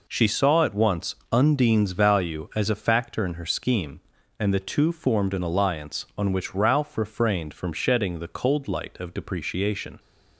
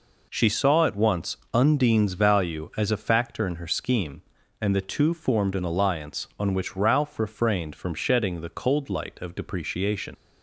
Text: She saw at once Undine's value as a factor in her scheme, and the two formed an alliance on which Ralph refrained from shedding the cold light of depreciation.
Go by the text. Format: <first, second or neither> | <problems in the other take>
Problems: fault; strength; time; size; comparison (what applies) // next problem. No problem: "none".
first | pauses between "once" and "Undine's"; slight; at 1.3 s; 0.18 s long; slight in the first // leaves "depreciation" unfinished; at 10.1 s; 60 ms